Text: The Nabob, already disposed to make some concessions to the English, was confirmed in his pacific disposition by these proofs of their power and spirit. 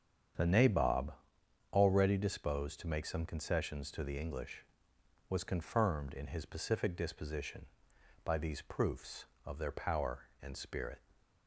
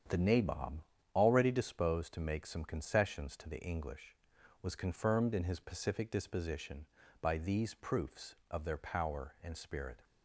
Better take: neither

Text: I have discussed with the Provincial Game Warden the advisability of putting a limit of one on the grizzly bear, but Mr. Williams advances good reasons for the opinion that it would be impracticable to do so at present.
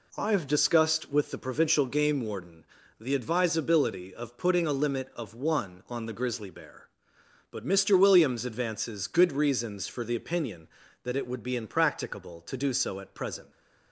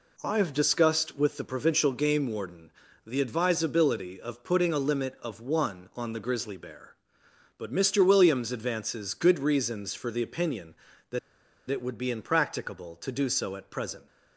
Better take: first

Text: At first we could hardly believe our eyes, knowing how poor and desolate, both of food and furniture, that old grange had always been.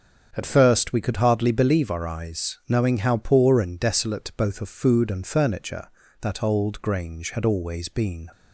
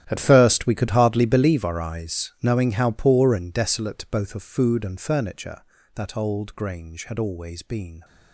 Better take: first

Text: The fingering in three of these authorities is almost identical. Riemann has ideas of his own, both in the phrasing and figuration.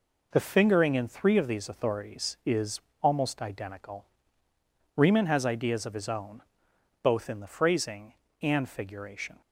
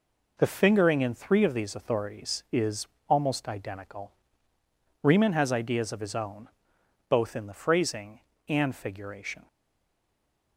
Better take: first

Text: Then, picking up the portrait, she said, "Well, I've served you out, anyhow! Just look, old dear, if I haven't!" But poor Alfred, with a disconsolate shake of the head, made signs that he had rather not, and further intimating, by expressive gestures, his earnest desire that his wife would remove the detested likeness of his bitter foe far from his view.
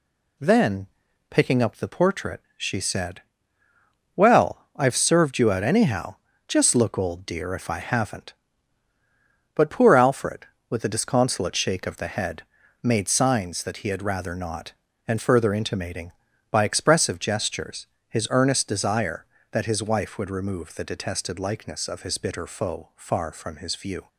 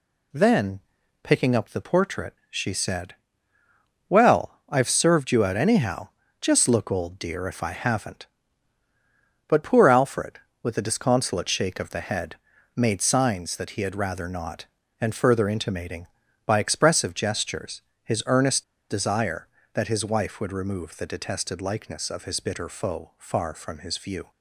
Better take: first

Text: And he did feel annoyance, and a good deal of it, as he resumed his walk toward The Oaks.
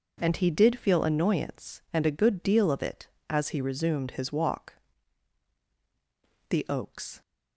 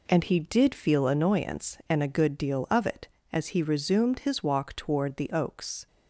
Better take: second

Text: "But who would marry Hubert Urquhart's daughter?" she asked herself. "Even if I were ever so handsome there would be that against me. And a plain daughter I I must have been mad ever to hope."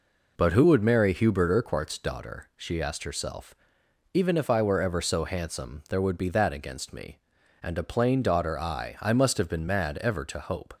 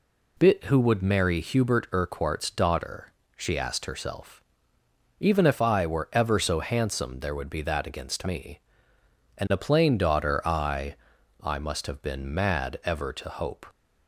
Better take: first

